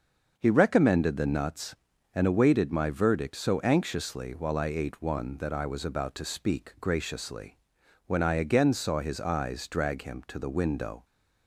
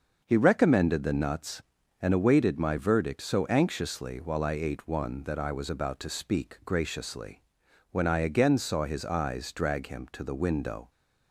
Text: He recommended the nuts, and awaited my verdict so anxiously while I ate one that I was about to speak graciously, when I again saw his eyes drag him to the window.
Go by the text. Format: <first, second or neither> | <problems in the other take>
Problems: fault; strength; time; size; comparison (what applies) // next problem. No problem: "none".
neither | starts louder than the rest; the same in both